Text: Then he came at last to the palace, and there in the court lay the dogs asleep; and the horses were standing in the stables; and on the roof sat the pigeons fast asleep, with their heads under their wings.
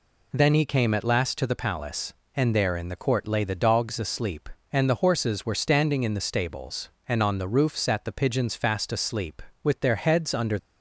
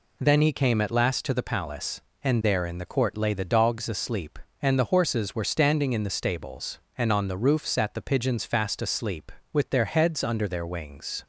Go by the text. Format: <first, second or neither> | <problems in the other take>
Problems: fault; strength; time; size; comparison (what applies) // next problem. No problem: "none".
second | stops before "their wings"; at 10.5 s